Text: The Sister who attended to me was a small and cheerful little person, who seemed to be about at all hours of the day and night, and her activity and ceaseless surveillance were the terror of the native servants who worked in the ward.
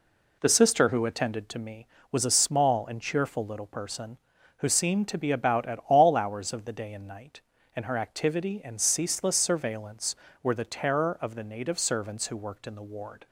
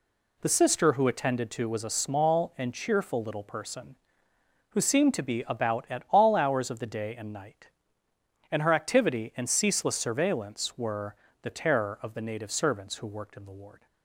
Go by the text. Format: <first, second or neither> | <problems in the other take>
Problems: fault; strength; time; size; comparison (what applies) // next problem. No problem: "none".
first | skips "me"; at 1.6 s // pauses between "were" and "the"; slight; at 11.1 s; 0.26 s long